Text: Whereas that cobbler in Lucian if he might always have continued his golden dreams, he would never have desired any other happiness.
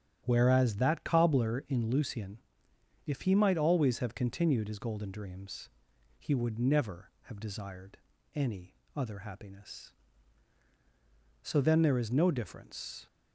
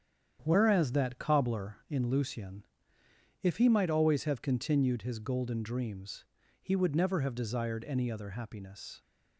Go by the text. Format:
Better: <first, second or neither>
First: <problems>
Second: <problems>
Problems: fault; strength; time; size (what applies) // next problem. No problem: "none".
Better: second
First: starts louder than the rest; strong; until 1.2 s; 10 dB // pauses between "Lucian" and "if"; noticeable; at 2.3 s; 0.68 s long // pauses between "desired" and "any"; slight; at 7.9 s; 0.36 s long // pauses between "any" and "other"; slight; at 8.7 s; 0.20 s long // goes on to say "So then there is no difference"; from 11.4 s on; 1.6 s long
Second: starts louder than the rest; strong; until 1.4 s; 8.5 dB // pauses between "Lucian" and "if"; noticeable; at 2.6 s; 0.78 s long